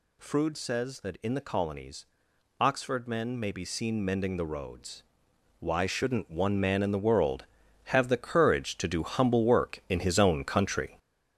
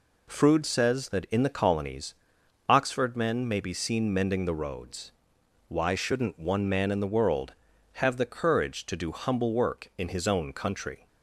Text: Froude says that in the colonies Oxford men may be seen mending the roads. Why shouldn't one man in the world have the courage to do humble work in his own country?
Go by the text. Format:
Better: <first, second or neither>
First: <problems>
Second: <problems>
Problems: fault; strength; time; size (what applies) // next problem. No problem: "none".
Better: second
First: gets louder; noticeable; throughout; 6 dB // pauses between "colonies" and "Oxford"; noticeable; at 2.0 s; 0.56 s long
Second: pauses between "colonies" and "Oxford"; noticeable; at 2.1 s; 0.56 s long